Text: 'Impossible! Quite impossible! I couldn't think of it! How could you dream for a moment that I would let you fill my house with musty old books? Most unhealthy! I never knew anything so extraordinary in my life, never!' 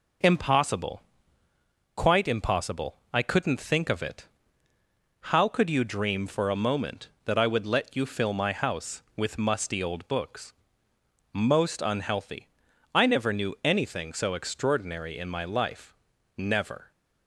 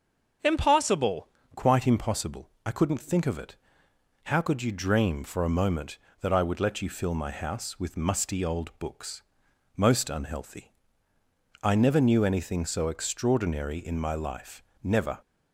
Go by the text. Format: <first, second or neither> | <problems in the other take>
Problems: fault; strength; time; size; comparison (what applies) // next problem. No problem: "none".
first | starts louder than the rest; until 1.6 s; 7 dB // changes voice at "Quite"; from 1.5 s on; 13.6 s long